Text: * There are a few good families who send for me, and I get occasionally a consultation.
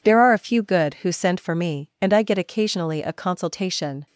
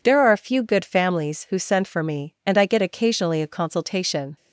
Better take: second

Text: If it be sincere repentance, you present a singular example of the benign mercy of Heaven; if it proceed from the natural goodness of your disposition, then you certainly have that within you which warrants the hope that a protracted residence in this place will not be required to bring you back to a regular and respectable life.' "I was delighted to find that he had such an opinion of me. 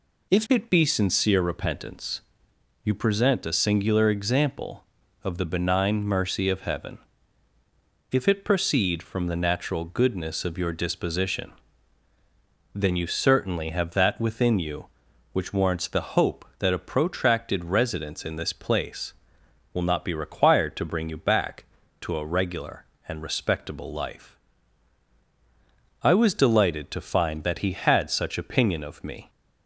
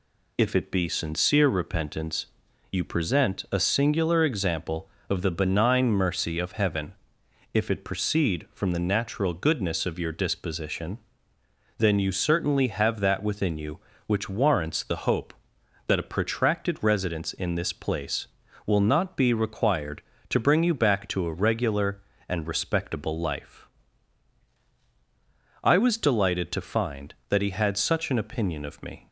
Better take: second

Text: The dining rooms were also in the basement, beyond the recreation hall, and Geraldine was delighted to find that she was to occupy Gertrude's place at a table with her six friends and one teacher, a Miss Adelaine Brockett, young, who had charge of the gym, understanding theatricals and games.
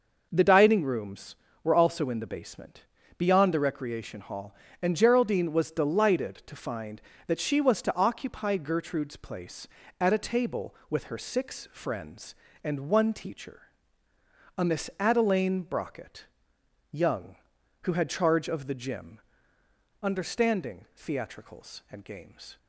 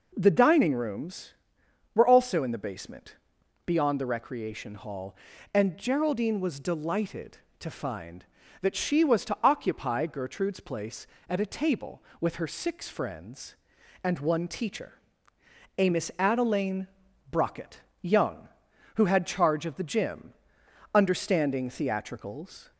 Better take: first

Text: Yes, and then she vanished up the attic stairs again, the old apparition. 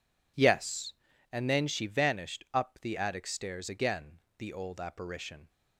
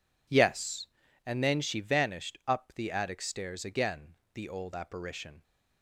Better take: neither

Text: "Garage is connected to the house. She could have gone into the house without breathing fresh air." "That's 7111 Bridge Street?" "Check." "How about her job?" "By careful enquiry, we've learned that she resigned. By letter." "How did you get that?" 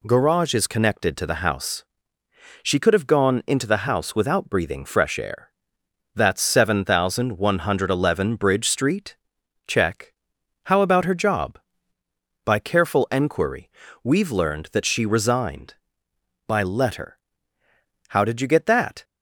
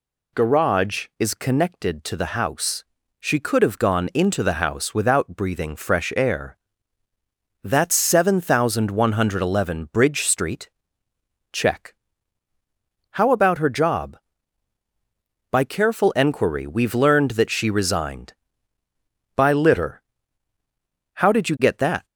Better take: first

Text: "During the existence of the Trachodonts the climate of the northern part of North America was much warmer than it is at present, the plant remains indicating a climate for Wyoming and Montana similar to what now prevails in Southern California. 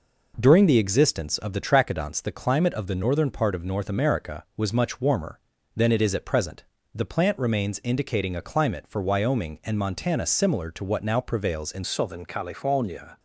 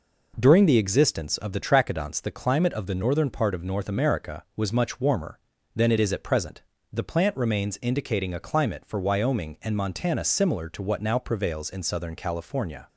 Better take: second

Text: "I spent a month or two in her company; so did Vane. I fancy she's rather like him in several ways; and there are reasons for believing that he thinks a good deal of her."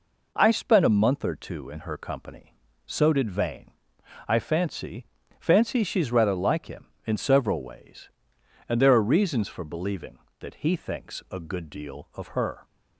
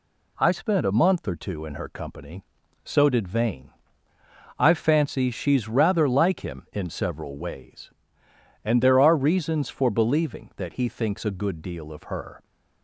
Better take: second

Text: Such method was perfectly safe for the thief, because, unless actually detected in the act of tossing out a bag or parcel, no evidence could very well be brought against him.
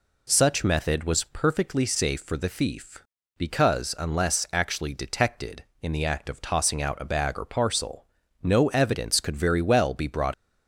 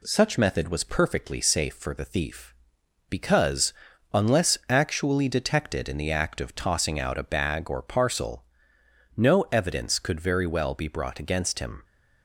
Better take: second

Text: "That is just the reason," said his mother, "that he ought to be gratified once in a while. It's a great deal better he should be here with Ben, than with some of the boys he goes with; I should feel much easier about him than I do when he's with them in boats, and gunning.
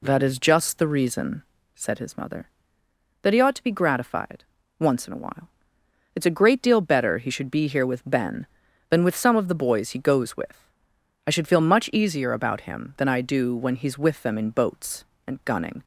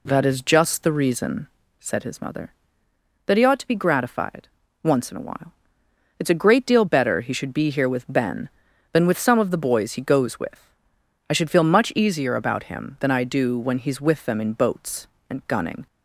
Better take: neither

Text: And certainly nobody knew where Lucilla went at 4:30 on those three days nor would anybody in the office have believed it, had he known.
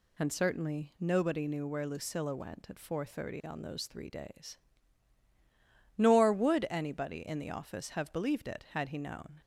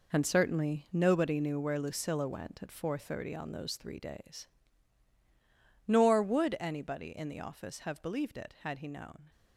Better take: first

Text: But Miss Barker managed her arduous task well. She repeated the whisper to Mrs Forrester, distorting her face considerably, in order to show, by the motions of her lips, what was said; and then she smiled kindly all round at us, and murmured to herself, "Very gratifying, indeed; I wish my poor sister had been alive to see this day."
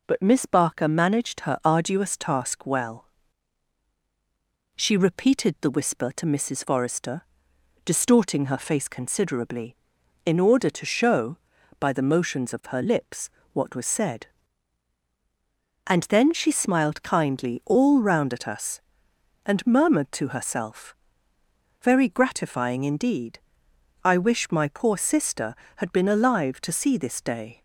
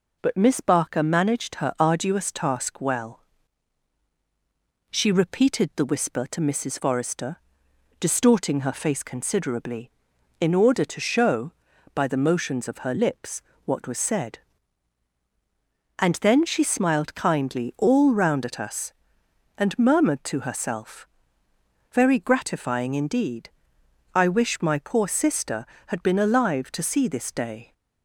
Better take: neither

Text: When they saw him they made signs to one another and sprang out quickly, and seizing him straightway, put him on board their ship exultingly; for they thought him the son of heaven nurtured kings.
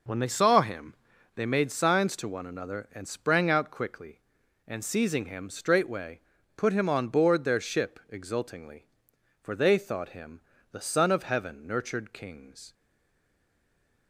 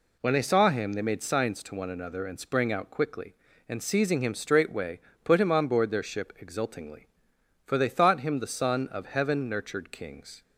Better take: second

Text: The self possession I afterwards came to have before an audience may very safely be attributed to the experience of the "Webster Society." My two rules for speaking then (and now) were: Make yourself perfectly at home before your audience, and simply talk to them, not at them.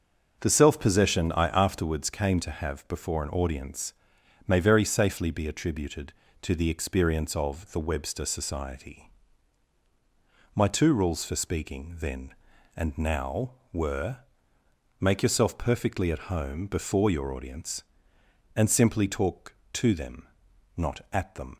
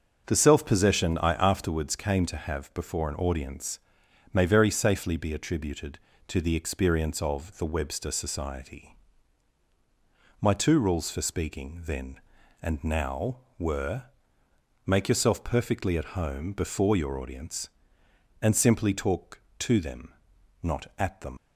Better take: first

